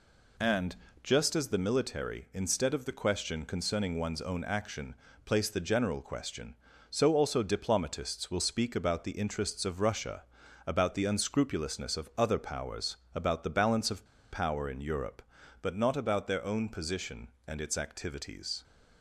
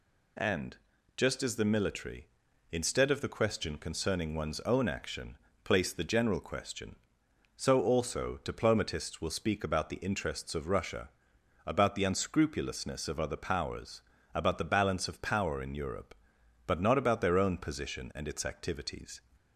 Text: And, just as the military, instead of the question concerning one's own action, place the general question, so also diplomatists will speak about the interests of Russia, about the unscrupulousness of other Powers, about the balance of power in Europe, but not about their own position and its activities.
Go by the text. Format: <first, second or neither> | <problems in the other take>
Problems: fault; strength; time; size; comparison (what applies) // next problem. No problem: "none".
second | pauses between "of" and "power"; slight; at 14.0 s; 0.26 s long